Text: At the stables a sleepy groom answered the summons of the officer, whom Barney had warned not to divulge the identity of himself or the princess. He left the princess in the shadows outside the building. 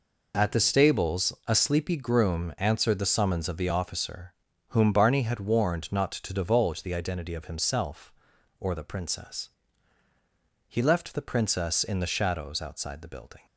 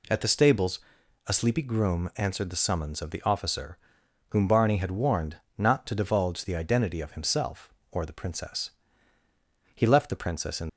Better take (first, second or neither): first